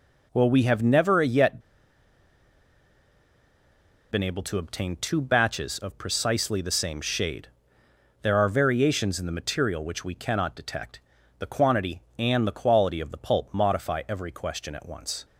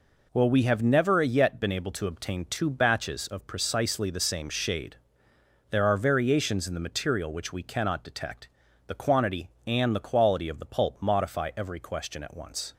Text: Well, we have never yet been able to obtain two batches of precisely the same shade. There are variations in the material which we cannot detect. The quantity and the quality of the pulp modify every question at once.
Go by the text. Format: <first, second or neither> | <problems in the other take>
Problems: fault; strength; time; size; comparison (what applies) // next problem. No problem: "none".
second | pauses between "yet" and "been"; strong; at 1.6 s; 2.5 s long